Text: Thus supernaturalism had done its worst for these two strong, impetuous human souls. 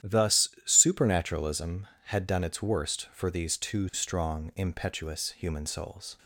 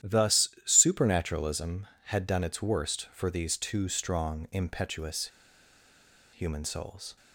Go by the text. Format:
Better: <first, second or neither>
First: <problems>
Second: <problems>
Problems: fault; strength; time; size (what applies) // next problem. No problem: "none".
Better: first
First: starts louder than the rest; strong; until 1.2 s; 11.5 dB // pauses between "Thus" and "supernaturalism"; slight; at 0.4 s; 0.16 s long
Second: starts louder than the rest; strong; until 1.2 s; 11.5 dB // pauses between "Thus" and "supernaturalism"; slight; at 0.4 s; 0.16 s long // pauses between "impetuous" and "human"; at 5.2 s; 1.0 s long